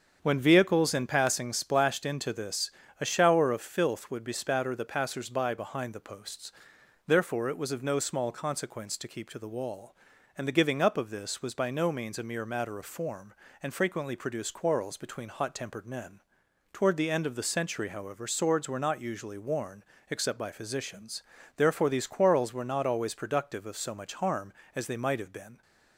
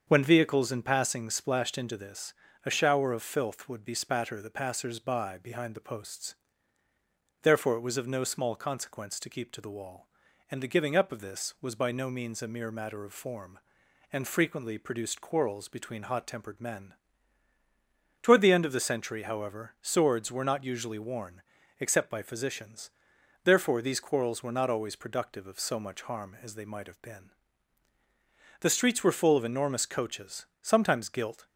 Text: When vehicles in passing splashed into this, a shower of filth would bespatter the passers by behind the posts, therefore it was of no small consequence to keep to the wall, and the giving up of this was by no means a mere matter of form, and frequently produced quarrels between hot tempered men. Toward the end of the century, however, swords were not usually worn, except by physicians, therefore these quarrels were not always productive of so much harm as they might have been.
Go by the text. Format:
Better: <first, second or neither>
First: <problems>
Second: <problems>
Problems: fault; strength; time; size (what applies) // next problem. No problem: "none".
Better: first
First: starts louder than the rest; strong; until 1.2 s; 7 dB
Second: starts louder than the rest; strong; until 1.0 s; 7 dB // goes on to say "The streets were full of enormous coaches sometimes gilt"; strong; from 28.6 s on; 2.8 s long